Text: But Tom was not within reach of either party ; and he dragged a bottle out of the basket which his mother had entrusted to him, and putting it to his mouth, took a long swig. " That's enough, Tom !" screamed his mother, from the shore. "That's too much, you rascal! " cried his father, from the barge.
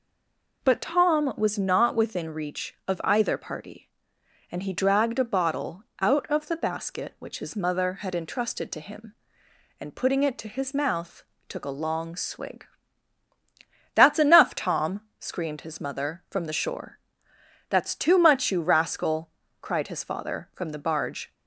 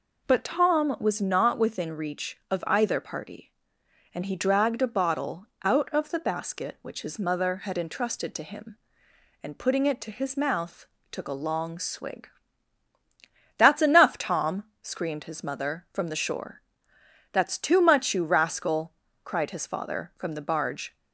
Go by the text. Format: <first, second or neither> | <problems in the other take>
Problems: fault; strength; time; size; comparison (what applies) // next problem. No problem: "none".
second | stays silent before the first word; slight; until 0.6 s; 0.6 s long // pauses between "bottle" and "out"; slight; at 5.8 s; 0.16 s long; slight in the second